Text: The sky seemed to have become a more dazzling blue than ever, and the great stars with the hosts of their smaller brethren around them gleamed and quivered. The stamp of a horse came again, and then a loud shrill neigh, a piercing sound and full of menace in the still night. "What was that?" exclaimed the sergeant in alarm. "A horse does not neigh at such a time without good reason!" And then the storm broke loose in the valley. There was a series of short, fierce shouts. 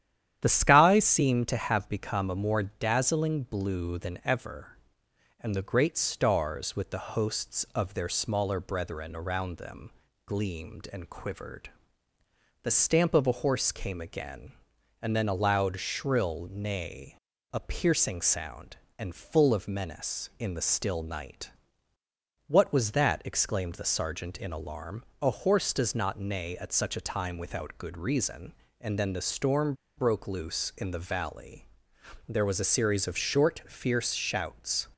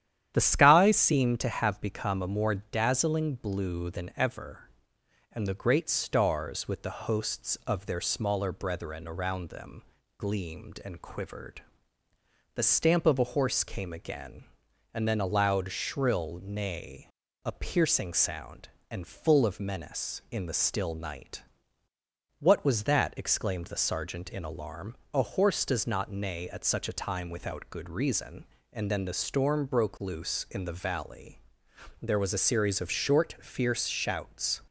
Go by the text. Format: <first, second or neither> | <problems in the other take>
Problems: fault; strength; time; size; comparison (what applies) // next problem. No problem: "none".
second | starts louder than the rest; strong; until 1.4 s; 10.5 dB; strong in the second // pauses between "them" and "gleamed"; slight; at 9.9 s; 0.34 s long; slight in the second // pauses between "storm" and "broke"; slight; at 29.7 s; 0.23 s long